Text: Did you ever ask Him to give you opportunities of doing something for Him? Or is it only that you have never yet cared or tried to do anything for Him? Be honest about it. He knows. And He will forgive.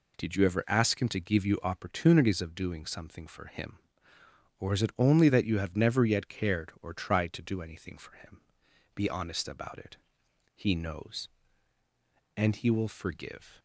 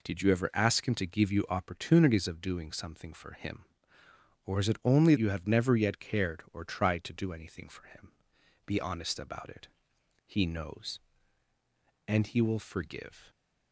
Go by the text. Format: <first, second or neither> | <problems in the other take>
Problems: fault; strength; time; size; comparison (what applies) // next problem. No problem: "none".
first | skips "that"; at 5.1 s